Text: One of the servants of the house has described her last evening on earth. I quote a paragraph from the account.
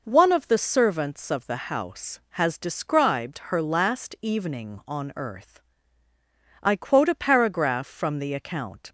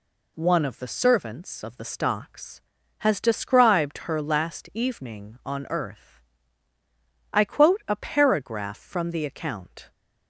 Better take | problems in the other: first | says "stocks" for "house"; at 1.8 s

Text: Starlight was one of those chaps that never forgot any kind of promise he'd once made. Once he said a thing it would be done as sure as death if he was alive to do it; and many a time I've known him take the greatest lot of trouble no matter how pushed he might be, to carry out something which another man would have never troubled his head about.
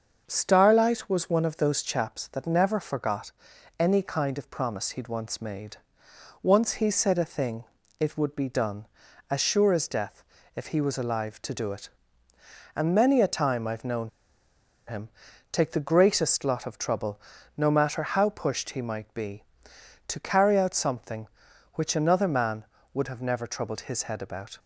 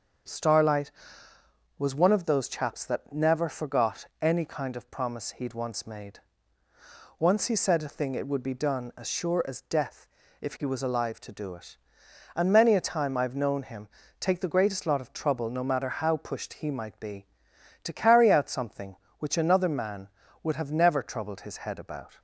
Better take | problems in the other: second | starts louder than the rest; until 1.2 s; 6.5 dB; strong in the second // pauses between "forgot" and "any"; at 3.3 s; 0.44 s long // pauses between "thing" and "it"; slight; at 7.6 s; 0.34 s long // pauses between "death" and "if"; slight; at 10.2 s; 0.32 s long; slight in the second // pauses between "known" and "him"; noticeable; at 14.0 s; 0.78 s long // pauses between "him" and "take"; at 15.0 s; 0.42 s long; slight in the second // pauses between "trouble" and "no"; at 17.1 s; 0.38 s long

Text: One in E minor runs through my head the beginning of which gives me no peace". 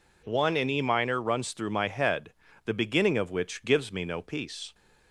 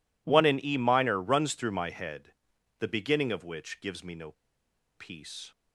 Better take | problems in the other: first | pauses between "head" and "the"; noticeable; at 2.3 s; 0.46 s long; slight in the first // pauses between "no" and "peace"; noticeable; at 4.3 s; 0.64 s long

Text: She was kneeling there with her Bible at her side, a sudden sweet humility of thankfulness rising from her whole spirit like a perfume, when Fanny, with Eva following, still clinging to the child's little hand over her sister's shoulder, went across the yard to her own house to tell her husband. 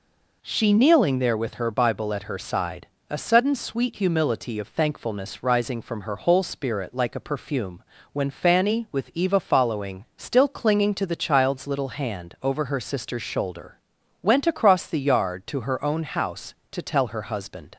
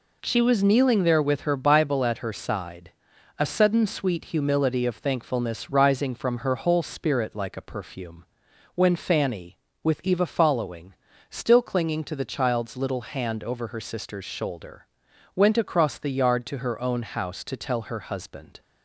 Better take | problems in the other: second | skips "was"; at 0.7 s

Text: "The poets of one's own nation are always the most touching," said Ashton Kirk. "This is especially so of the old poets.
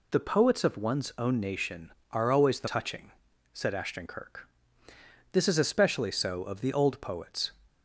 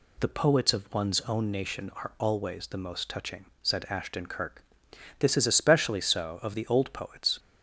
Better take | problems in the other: second | skips "most"; at 2.6 s

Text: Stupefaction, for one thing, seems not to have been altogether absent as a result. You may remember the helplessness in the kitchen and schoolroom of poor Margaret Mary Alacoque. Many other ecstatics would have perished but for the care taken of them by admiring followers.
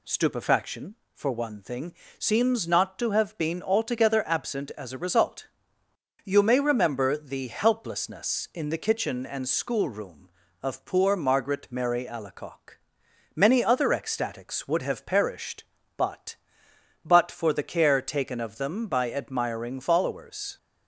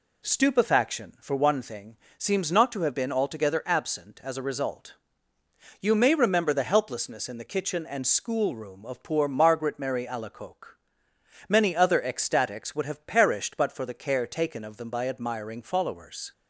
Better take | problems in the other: second | says "but" twice; at 17.0 s

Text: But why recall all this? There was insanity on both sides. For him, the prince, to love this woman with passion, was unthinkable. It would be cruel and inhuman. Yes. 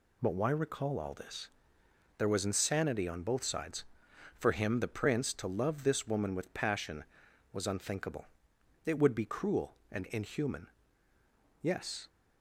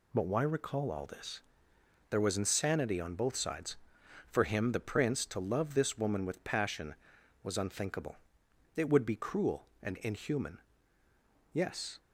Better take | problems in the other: neither | none

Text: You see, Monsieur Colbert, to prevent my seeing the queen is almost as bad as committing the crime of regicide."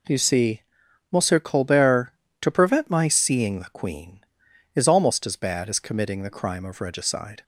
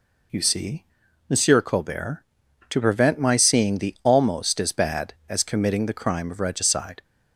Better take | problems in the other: first | skips "queen is"; at 3.9 s

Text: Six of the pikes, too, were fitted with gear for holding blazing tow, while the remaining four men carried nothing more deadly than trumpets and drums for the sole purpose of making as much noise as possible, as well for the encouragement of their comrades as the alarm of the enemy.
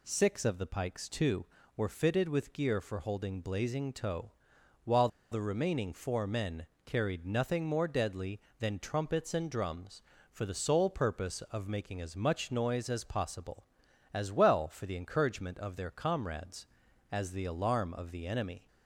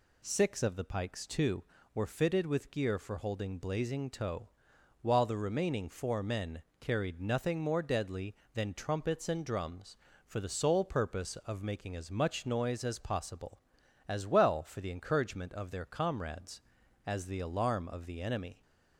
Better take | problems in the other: second | pauses between "while" and "the"; slight; at 5.0 s; 0.24 s long // pauses between "men" and "carried"; slight; at 6.6 s; 0.18 s long; slight in the second

